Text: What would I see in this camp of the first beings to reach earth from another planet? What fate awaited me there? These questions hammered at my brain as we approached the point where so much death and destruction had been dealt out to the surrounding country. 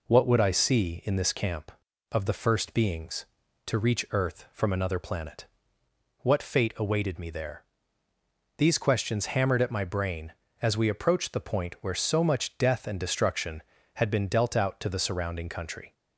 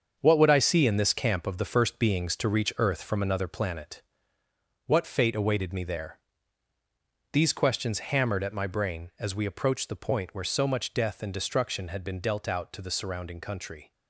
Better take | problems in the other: first | gets quieter; strong; throughout; 8.5 dB

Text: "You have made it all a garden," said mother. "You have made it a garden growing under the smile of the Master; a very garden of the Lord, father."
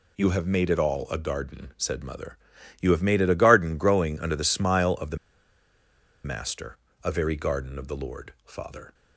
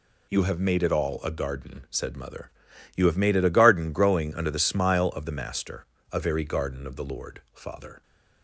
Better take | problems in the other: second | pauses between "the" and "Master"; at 5.1 s; 1.0 s long

